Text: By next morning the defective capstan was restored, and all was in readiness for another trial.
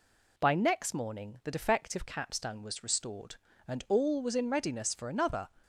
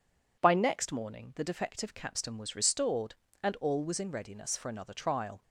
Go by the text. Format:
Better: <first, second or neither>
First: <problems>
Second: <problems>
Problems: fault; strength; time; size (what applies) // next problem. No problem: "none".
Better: second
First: stops before "trial"; at 5.6 s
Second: none